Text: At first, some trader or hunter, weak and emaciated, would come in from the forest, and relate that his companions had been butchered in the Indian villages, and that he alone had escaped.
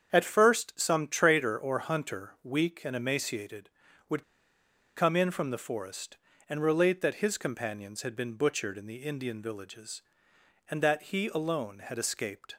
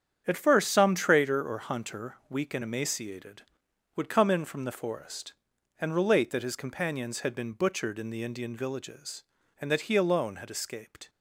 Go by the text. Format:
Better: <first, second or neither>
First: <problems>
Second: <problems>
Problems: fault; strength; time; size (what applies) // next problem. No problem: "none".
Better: second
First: starts louder than the rest; strong; until 1.1 s; 7.5 dB // pauses between "would" and "come"; noticeable; at 4.2 s; 0.73 s long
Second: starts louder than the rest; strong; until 1.2 s; 8.5 dB